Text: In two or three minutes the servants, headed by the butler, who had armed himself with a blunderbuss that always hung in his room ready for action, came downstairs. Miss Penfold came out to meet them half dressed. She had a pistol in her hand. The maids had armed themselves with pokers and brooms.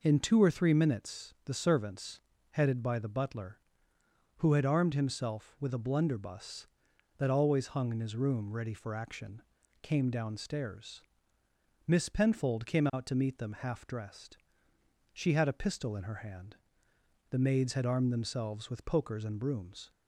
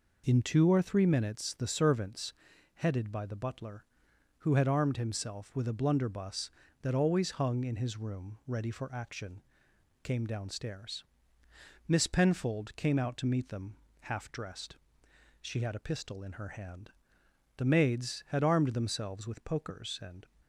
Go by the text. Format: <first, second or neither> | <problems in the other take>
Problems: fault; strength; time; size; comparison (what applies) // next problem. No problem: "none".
first | pauses between "them" and "half"; slight; at 13.7 s; 0.28 s long // stops before "brooms"; at 20.4 s